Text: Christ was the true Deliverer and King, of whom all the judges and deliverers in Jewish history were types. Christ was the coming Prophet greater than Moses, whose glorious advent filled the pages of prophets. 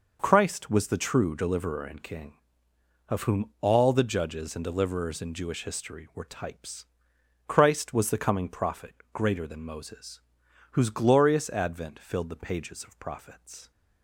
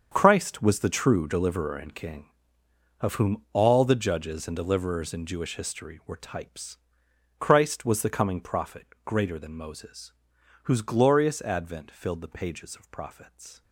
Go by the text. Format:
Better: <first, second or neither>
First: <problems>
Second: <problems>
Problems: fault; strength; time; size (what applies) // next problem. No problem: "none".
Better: first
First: pauses between "Prophet" and "greater"; slight; at 8.9 s; 0.20 s long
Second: gets quieter; strong; throughout; 13 dB // pauses between "Prophet" and "greater"; slight; at 8.8 s; 0.20 s long